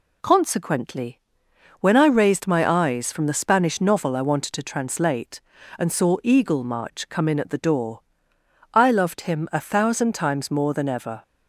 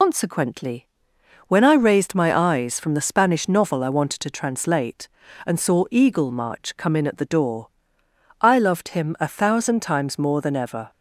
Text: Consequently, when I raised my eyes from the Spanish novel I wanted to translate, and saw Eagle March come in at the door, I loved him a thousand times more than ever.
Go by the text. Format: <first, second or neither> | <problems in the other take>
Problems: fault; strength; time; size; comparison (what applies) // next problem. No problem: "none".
first | loses the start of "Consequently"; at 0.0 s; 110 ms